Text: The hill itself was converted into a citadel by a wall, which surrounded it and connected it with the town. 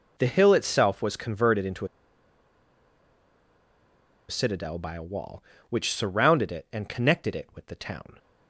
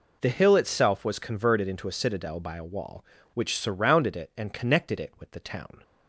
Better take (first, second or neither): second